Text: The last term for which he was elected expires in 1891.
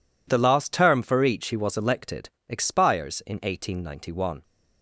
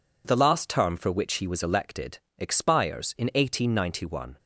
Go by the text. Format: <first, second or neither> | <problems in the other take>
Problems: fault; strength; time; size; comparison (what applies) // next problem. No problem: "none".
second | says "each" for "which"; at 1.2 s // pauses between "elected" and "expires"; slight; at 2.2 s; 0.22 s long; slight in the second